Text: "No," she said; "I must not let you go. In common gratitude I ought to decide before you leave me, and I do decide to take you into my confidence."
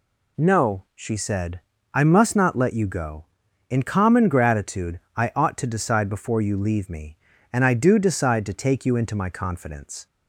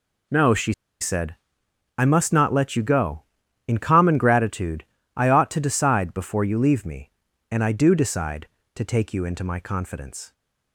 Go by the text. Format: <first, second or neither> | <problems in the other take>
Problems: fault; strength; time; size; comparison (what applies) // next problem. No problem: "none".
first | pauses between "she" and "said"; slight; at 0.7 s; 0.28 s long // pauses between "gratitude" and "I"; slight; at 4.8 s; 0.32 s long; slight in the first